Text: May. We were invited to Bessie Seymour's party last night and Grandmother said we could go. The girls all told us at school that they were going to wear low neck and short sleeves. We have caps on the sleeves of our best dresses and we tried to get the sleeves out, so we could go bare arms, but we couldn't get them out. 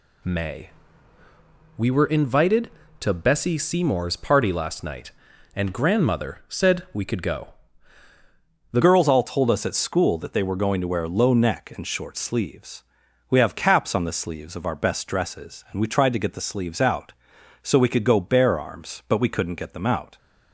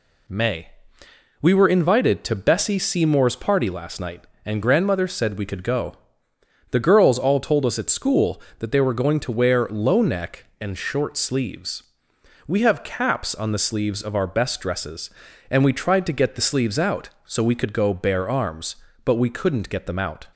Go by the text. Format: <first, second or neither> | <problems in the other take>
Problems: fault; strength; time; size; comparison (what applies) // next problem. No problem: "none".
second | changes voice at "girls"; from 8.8 s on; 11.3 s long